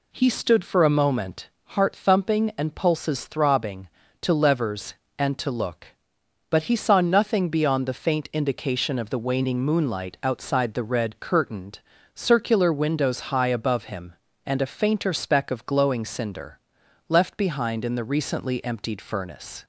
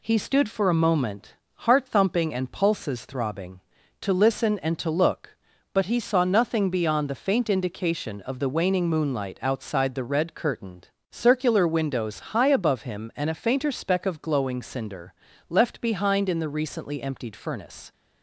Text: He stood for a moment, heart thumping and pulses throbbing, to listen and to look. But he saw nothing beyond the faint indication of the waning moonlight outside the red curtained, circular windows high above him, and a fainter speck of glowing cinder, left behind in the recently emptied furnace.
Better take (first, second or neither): second